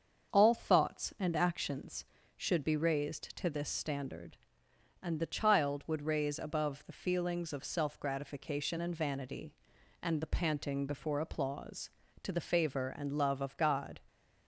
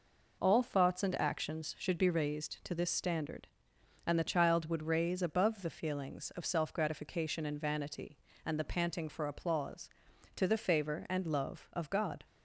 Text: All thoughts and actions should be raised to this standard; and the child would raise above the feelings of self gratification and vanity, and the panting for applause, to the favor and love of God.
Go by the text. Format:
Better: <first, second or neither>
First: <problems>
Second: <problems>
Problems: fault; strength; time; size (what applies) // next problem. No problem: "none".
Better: second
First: starts louder than the rest; until 1.3 s; 7 dB // says "before" for "for"; at 10.8 s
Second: none